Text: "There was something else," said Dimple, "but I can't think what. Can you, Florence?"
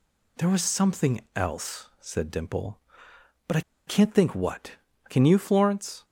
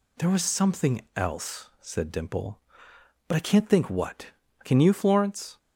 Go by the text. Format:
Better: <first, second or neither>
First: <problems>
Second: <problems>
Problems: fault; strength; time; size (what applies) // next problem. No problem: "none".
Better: second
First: pauses between "something" and "else"; slight; at 1.2 s; 0.16 s long // pauses between "I" and "can't"; slight; at 3.6 s; 0.27 s long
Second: pauses between "something" and "else"; slight; at 1.0 s; 0.16 s long